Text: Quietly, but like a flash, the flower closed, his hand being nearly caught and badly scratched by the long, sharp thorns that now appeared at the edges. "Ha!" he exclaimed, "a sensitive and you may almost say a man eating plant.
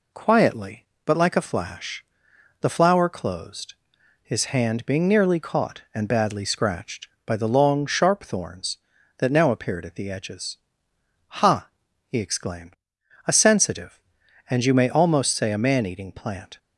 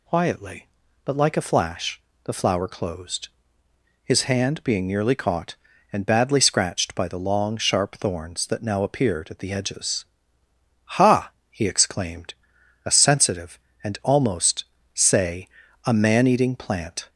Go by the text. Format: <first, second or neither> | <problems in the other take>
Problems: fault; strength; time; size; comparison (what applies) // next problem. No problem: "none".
first | skips "you may"; at 13.9 s // pauses between "almost" and "say"; slight; at 14.6 s; 0.30 s long // pauses between "say" and "a"; slight; at 15.4 s; 0.34 s long